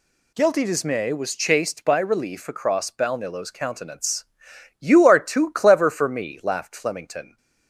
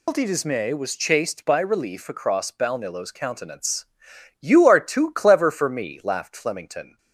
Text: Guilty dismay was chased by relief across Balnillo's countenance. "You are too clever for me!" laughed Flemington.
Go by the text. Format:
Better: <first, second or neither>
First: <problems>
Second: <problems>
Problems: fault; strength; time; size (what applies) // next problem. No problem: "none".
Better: first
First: none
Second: loses the start of "Guilty"; at 0.0 s; 125 ms